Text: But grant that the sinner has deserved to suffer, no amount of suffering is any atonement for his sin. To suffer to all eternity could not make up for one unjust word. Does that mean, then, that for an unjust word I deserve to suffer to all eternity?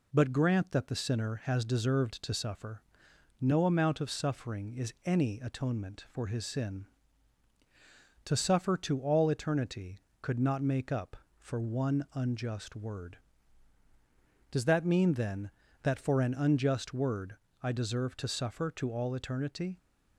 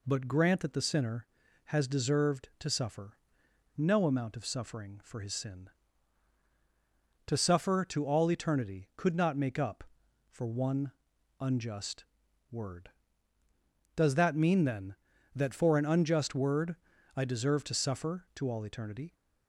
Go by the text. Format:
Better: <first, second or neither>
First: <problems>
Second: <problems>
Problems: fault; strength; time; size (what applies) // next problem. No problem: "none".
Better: first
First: pauses between "word" and "I"; slight; at 17.3 s; 0.26 s long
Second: skips "is any atonement"; at 5.0 s // pauses between "one" and "unjust"; noticeable; at 10.9 s; 0.48 s long // pauses between "unjust" and "word"; noticeable; at 12.0 s; 0.48 s long // pauses between "word" and "I"; at 16.7 s; 0.40 s long